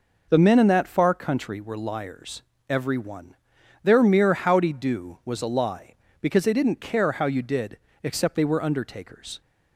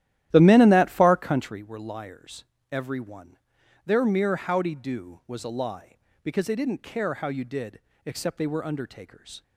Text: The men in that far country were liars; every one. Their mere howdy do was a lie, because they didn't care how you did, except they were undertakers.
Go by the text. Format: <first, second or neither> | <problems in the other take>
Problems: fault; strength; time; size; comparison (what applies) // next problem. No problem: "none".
first | starts louder than the rest; strong; until 1.6 s; 13 dB